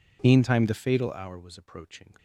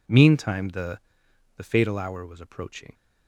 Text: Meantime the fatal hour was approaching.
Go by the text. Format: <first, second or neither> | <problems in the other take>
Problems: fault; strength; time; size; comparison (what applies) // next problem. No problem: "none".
first | says "the" twice; at 1.5 s